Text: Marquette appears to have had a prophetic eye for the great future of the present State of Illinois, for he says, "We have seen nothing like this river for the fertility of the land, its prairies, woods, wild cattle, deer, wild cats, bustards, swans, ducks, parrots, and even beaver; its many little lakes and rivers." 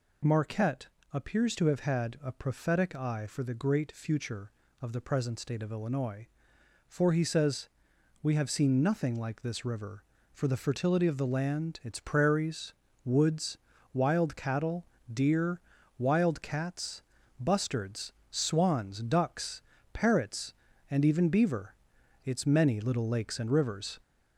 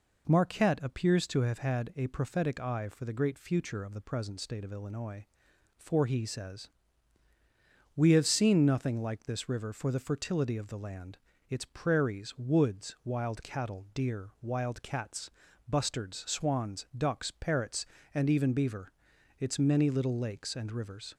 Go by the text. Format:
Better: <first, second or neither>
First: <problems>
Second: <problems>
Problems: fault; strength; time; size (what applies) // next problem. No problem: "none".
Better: second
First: gets louder; slight; throughout; 3.5 dB // pauses between "Marquette" and "appears"; slight; at 0.8 s; 0.24 s long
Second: none